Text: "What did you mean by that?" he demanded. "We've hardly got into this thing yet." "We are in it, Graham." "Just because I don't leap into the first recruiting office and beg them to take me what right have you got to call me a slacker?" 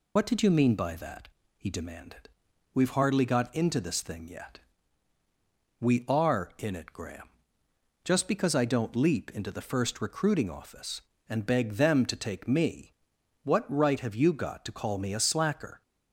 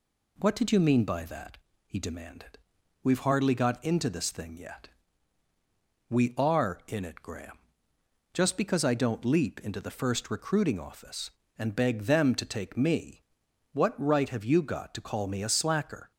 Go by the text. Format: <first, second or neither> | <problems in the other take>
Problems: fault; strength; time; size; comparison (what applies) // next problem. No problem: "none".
second | loses the start of "What"; at 0.1 s; 70 ms // pauses between "me" and "what"; noticeable; at 12.9 s; 0.50 s long; noticeable in the second